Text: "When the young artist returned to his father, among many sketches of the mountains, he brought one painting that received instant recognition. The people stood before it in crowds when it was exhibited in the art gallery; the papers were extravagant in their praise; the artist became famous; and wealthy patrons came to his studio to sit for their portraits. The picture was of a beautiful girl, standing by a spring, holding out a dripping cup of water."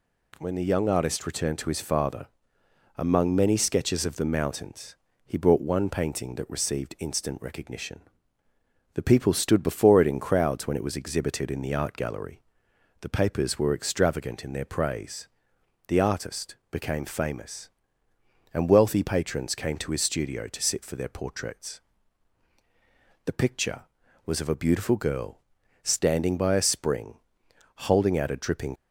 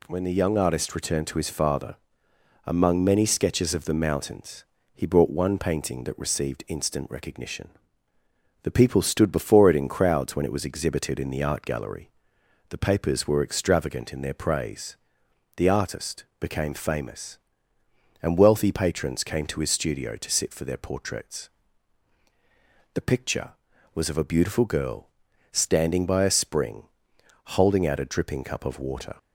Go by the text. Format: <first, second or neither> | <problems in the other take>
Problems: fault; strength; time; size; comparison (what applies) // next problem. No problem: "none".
second | pauses between "artist" and "became"; slight; at 16.5 s; 0.16 s long; slight in the second // stops before "cup of water"; at 28.7 s